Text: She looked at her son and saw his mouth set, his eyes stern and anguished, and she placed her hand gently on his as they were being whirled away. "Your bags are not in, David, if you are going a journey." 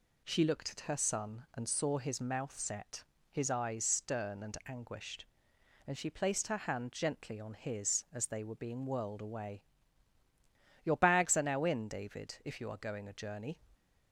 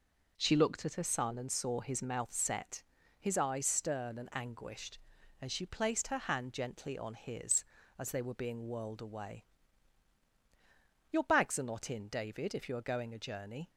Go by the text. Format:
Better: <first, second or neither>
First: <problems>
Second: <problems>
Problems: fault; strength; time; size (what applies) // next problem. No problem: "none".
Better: second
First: says "now" for "not"; at 11.4 s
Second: none